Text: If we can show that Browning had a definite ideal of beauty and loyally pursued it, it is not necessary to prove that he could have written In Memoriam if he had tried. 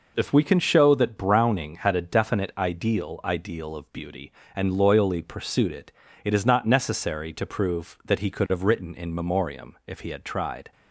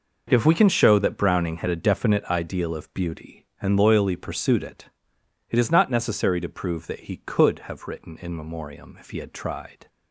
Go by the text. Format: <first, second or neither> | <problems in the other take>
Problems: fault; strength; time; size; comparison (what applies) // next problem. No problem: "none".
second | says "ideal" twice; at 3.2 s